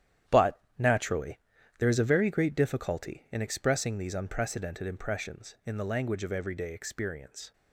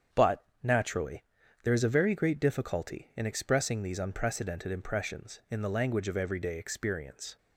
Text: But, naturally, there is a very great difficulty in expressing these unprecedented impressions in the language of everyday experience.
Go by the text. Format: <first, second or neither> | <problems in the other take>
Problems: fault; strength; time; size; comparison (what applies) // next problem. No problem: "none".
second | gets quieter; strong; throughout; 9.5 dB // starts louder than the rest; strong; until 1.8 s; 10.5 dB; strong in the second